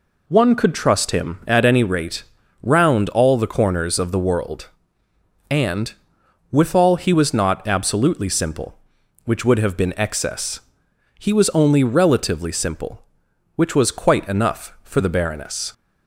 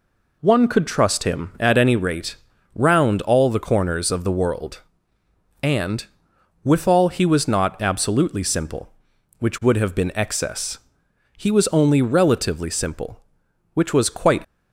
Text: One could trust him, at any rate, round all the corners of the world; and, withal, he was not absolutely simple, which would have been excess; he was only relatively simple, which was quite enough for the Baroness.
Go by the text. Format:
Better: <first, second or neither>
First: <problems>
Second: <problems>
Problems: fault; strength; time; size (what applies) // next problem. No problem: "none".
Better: first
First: none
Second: stops before "enough for the Baroness"; at 14.4 s